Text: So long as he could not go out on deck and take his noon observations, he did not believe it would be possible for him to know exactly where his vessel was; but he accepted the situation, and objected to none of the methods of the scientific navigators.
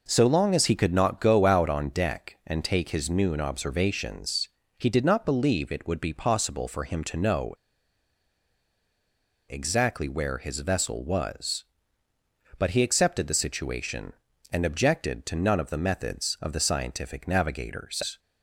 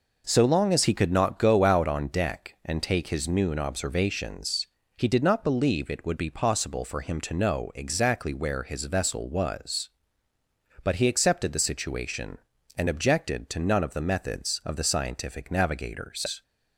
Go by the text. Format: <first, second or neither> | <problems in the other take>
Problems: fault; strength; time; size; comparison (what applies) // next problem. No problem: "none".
second | pauses between "know" and "exactly"; strong; at 7.5 s; 1.9 s long